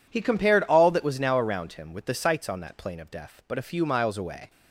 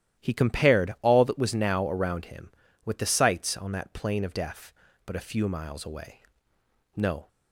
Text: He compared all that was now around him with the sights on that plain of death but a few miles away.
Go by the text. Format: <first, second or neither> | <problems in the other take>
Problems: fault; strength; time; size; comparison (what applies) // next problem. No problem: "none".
first | starts louder than the rest; strong; until 1.2 s; 12.5 dB // goes on to say "No"; slight; from 6.9 s on; 0.32 s long